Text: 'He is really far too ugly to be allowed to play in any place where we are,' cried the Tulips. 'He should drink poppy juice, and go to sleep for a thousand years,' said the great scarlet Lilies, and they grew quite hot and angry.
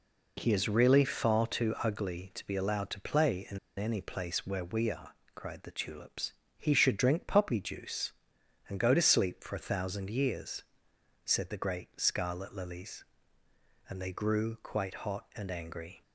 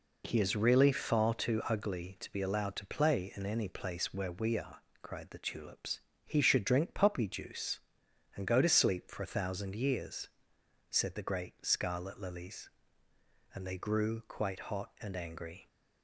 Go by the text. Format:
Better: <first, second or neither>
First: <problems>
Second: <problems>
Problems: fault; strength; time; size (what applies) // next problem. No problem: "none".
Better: second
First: pauses between "in" and "any"; slight; at 3.5 s; 0.18 s long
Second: none